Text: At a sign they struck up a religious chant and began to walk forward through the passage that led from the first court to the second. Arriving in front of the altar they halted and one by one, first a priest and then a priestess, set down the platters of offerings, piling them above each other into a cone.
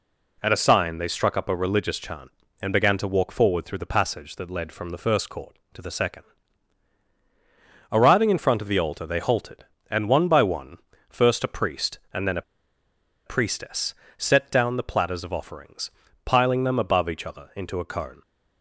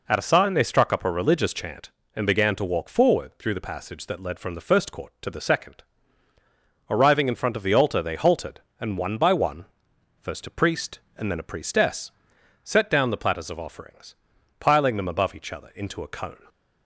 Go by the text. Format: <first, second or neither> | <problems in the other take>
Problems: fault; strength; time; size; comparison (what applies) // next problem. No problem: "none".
second | pauses between "a" and "priestess"; noticeable; at 12.4 s; 0.85 s long